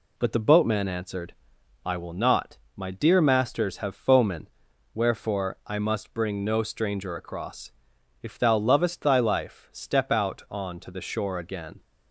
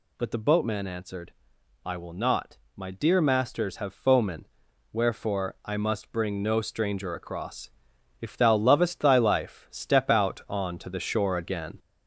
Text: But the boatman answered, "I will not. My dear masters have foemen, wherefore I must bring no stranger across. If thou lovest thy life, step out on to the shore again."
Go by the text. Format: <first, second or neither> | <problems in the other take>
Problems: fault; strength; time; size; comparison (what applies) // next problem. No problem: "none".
first | gets louder; noticeable; throughout; 4 dB